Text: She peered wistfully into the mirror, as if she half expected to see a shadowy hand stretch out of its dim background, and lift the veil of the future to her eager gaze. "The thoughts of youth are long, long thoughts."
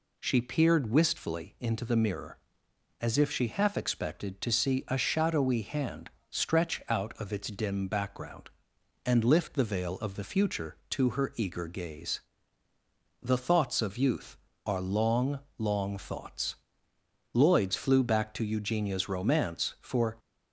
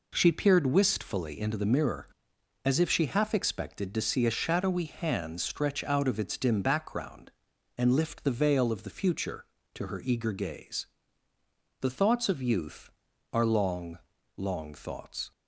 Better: second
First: pauses between "hand" and "stretch"; slight; at 6.0 s; 0.20 s long // goes on to say "Lloyd's flew back to Eugenia's romance for"; strong; from 17.3 s on; 2.8 s long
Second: none

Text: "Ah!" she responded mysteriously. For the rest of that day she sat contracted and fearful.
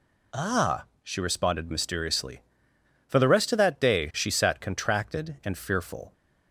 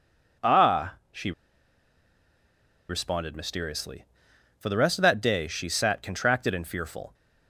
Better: first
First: none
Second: pauses between "she" and "responded"; strong; at 1.3 s; 1.5 s long

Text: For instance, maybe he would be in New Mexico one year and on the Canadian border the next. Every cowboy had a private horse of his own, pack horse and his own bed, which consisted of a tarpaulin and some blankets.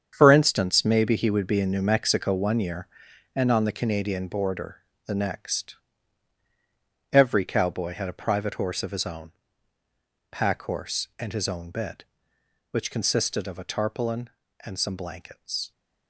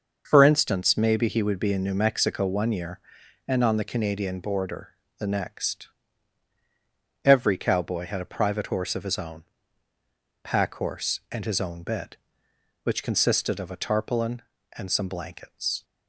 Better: second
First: gets quieter; strong; throughout; 11 dB // starts louder than the rest; strong; until 1.1 s; 7.5 dB // pauses between "border" and "the"; slight; at 4.8 s; 0.22 s long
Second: starts louder than the rest; until 1.2 s; 6 dB // pauses between "border" and "the"; slight; at 4.9 s; 0.22 s long

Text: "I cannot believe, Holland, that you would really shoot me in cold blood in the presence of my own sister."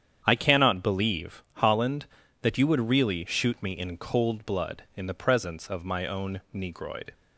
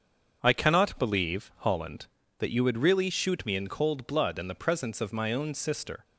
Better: second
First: starts louder than the rest; strong; until 1.2 s; 8.5 dB // says "negroid" for "sister"; at 6.5 s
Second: starts louder than the rest; until 1.4 s; 7 dB

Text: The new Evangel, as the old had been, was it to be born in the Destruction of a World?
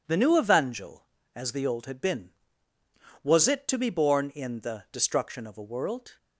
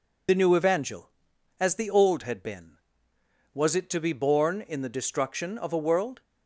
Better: first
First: none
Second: loses the start of "The"; at 0.2 s; 45 ms

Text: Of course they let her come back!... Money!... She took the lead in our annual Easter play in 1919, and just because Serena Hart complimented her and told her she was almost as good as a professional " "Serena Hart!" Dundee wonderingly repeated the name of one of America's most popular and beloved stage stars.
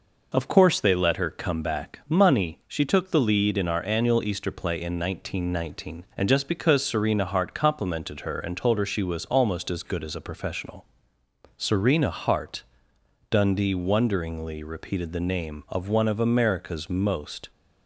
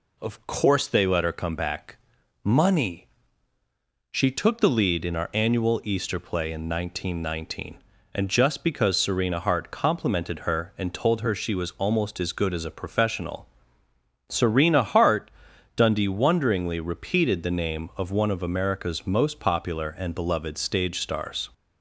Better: second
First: stops before "popular and beloved stage stars"; at 17.4 s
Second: none

